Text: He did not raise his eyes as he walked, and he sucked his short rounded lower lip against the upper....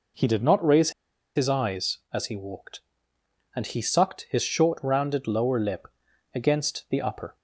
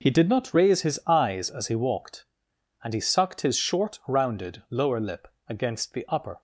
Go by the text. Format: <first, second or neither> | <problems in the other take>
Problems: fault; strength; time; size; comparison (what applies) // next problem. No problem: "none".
second | pauses between "raise" and "his"; at 0.9 s; 0.45 s long // pauses between "lip" and "against"; noticeable; at 5.8 s; 0.46 s long; slight in the second